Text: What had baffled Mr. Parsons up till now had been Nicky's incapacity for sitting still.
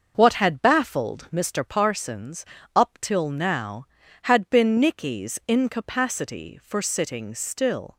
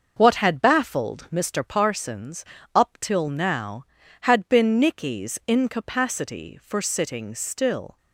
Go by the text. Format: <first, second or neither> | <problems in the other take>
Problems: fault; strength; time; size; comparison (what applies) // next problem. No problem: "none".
neither | starts louder than the rest; the same in both // pauses between "Parsons" and "up"; slight; the same in both